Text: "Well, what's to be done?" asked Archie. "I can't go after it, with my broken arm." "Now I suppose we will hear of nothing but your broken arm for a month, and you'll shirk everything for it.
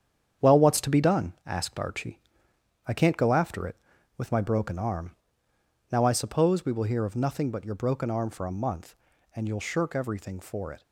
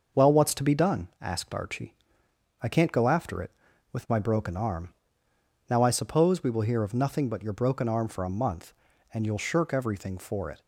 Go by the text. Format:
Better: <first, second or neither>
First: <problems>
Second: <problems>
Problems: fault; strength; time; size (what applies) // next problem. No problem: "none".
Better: second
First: gets quieter; strong; throughout; 7.5 dB // starts louder than the rest; strong; until 1.5 s; 8.5 dB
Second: starts louder than the rest; noticeable; until 1.3 s; 6 dB